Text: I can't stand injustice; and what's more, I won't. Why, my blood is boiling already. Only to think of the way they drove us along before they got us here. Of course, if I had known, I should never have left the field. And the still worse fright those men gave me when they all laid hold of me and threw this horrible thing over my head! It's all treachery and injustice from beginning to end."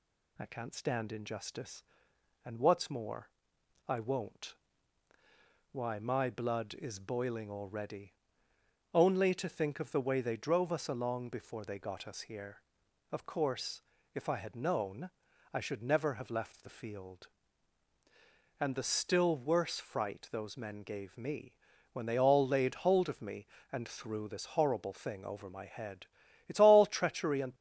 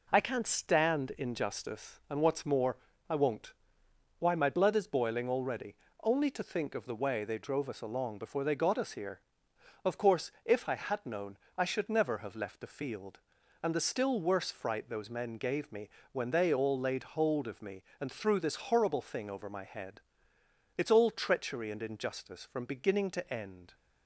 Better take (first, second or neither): second